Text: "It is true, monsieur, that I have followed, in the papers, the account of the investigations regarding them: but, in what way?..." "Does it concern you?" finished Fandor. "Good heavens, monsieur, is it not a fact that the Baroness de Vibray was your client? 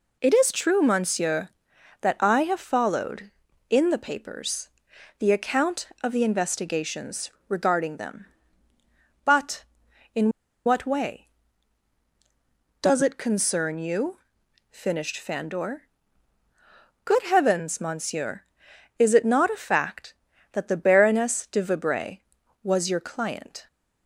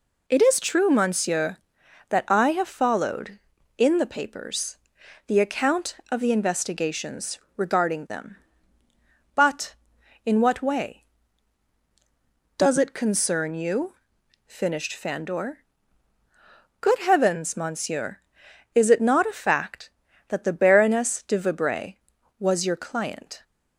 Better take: second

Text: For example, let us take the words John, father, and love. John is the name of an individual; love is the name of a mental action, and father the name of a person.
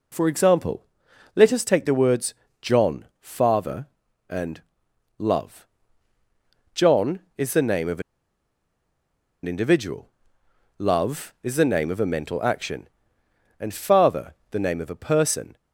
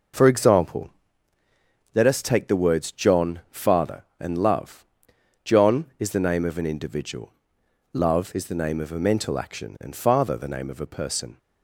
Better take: second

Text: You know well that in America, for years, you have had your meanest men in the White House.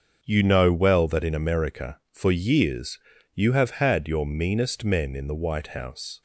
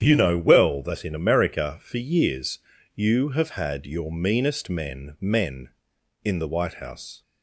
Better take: first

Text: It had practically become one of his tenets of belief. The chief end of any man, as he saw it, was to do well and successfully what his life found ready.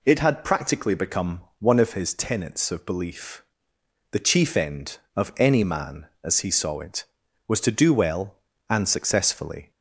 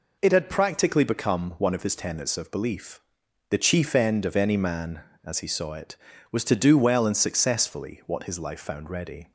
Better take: second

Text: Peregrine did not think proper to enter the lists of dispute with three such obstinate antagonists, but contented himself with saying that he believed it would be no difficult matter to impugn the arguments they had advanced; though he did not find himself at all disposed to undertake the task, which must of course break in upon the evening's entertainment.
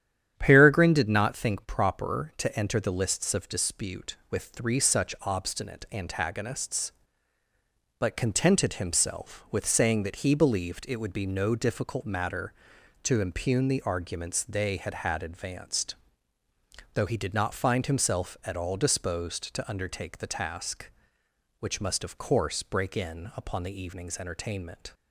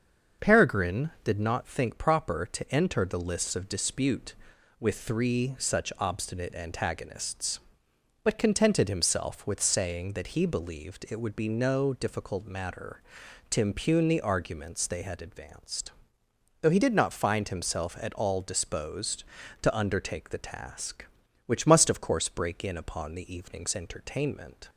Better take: second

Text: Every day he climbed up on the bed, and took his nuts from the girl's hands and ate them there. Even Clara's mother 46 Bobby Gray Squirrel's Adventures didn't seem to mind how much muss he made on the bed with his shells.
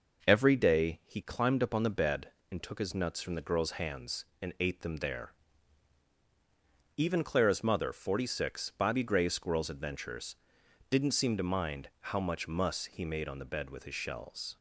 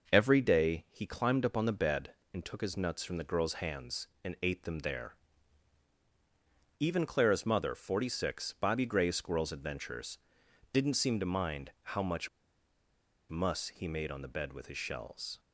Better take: first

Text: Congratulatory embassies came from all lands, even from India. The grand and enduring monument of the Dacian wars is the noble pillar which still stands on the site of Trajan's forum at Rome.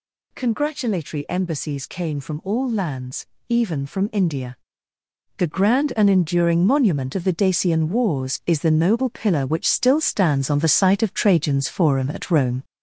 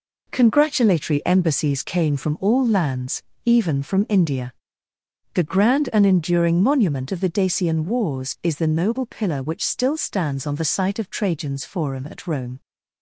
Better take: second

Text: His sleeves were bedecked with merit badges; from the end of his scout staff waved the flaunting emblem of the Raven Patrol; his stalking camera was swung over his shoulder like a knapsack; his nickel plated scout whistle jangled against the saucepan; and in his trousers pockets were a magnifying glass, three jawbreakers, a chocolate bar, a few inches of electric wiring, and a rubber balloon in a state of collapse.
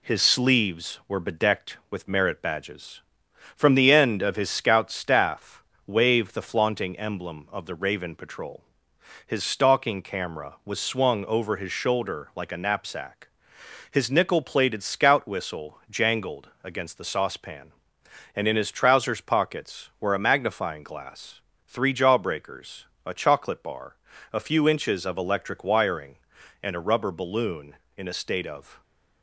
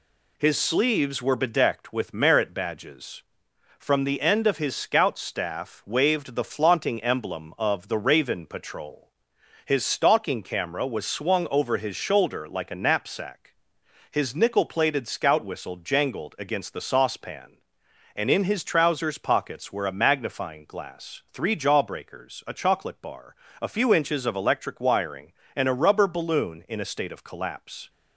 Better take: second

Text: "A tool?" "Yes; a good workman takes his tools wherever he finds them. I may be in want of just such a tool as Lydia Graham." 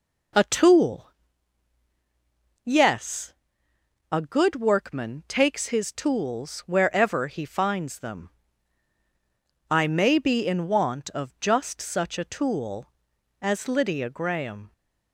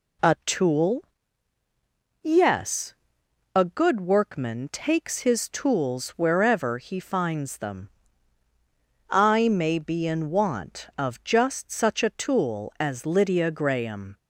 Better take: neither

